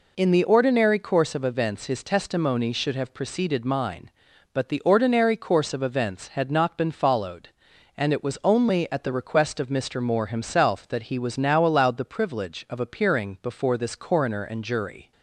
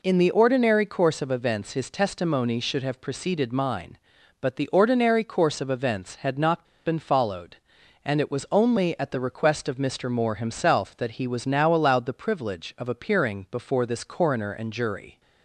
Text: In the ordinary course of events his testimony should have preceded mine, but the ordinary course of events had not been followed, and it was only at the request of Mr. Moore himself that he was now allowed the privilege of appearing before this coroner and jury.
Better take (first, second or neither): first